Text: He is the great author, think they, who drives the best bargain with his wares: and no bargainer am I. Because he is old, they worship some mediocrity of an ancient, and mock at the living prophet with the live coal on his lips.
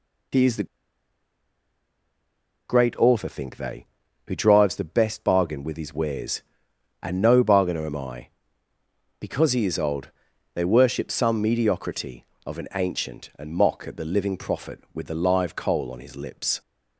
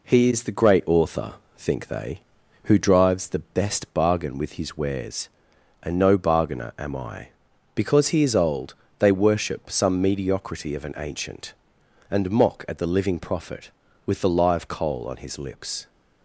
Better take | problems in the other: second | pauses between "the" and "great"; strong; at 0.6 s; 2.0 s long

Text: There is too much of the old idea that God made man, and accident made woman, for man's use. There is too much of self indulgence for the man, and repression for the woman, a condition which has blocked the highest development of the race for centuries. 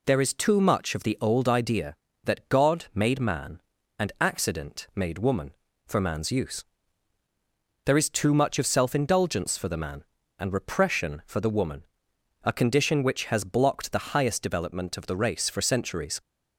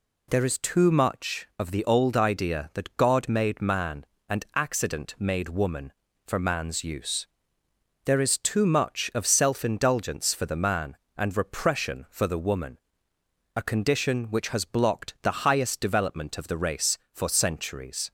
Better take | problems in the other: neither | none

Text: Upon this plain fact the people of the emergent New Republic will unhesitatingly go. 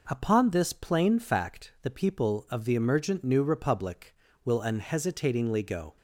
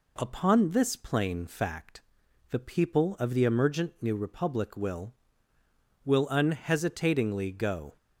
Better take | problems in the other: first | pauses between "fact" and "the"; noticeable; at 2.0 s; 0.48 s long // says "will" twice; at 6.0 s

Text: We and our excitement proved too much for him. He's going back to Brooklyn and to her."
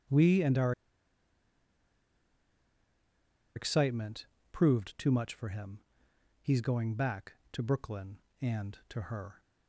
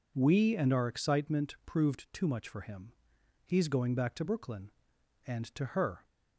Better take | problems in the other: second | starts louder than the rest; strong; until 3.9 s; 8.5 dB // pauses between "our" and "excitement"; strong; at 0.7 s; 2.8 s long // pauses between "excitement" and "proved"; slight; at 4.2 s; 0.26 s long

